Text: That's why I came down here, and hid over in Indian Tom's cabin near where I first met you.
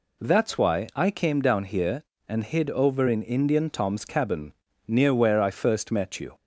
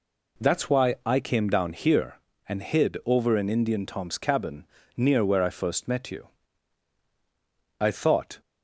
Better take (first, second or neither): first